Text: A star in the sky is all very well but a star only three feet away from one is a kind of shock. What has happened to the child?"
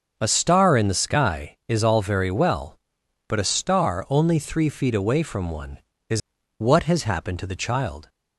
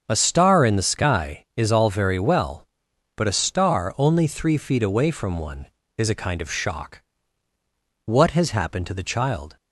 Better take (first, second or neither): second